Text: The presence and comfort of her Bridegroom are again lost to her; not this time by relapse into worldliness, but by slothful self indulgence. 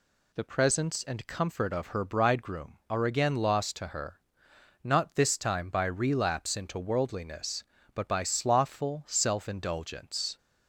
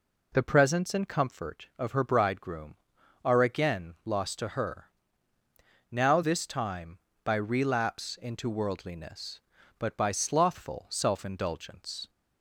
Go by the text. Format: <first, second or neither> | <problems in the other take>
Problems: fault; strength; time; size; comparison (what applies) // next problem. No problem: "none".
first | says "now" for "not"; at 5.9 s